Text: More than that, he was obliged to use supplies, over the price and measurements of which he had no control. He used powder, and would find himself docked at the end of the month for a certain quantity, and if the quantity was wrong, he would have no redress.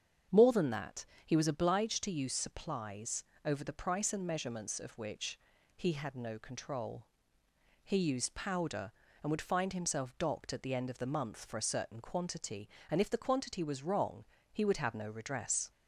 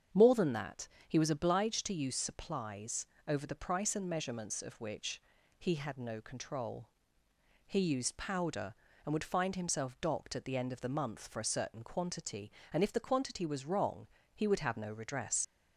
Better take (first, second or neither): first